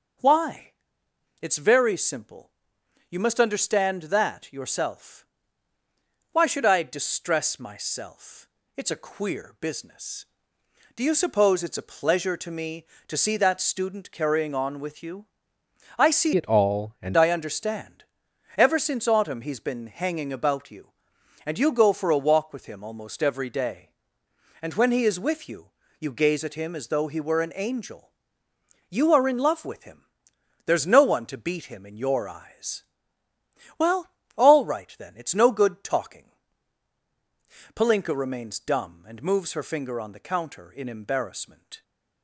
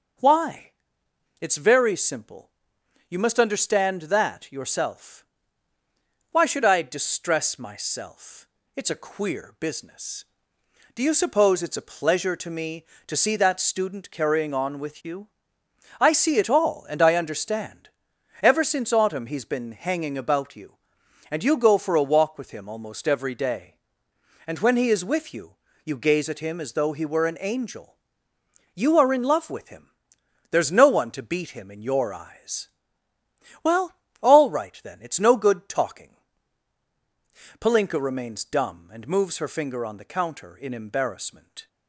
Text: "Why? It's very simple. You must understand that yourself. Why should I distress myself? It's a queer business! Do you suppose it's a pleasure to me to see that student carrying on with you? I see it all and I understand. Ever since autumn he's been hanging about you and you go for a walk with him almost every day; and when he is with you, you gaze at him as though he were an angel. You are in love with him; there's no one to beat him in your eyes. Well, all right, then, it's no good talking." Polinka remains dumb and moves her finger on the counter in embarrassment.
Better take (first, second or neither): second